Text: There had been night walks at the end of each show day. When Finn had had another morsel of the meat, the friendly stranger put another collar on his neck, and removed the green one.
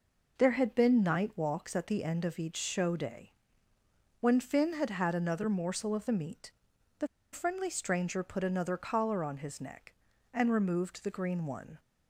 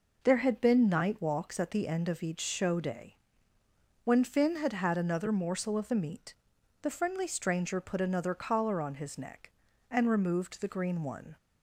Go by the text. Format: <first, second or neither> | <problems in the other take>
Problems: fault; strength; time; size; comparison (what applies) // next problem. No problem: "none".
second | pauses between "the" and "friendly"; slight; at 7.0 s; 0.25 s long